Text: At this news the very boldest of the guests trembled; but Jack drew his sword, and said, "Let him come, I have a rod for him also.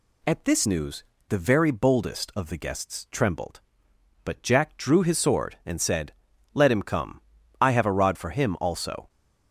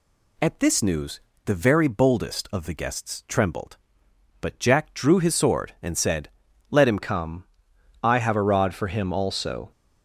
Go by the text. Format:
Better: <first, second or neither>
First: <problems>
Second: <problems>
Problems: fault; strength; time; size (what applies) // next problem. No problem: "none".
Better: first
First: pauses between "news" and "the"; slight; at 1.0 s; 0.26 s long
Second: pauses between "news" and "the"; slight; at 1.1 s; 0.26 s long // changes voice at "come"; from 7.0 s on; 2.7 s long